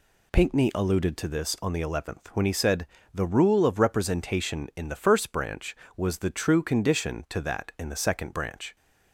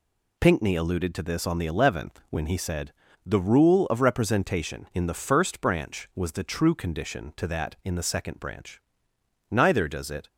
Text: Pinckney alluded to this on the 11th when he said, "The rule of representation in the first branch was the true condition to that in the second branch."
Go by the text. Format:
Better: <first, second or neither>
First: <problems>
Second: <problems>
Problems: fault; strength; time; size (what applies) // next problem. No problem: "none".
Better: first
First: none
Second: goes on to say "Neither does it"; noticeable; from 9.4 s on; 0.78 s long